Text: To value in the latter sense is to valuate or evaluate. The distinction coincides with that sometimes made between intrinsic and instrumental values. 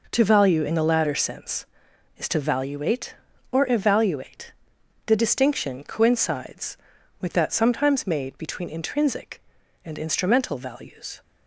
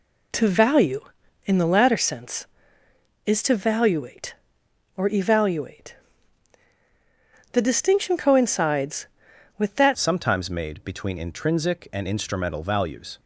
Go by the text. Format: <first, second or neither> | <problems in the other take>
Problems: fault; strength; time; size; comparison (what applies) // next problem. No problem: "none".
first | changes voice at "sometimes"; from 9.9 s on; 3.2 s long